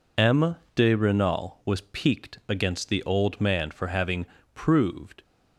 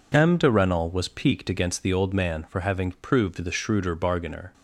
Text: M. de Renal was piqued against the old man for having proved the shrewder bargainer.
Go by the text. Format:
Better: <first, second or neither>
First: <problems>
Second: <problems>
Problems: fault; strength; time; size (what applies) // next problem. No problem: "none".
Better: second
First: pauses between "having" and "proved"; slight; at 4.2 s; 0.26 s long // stops before "the shrewder bargainer"; at 5.2 s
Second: none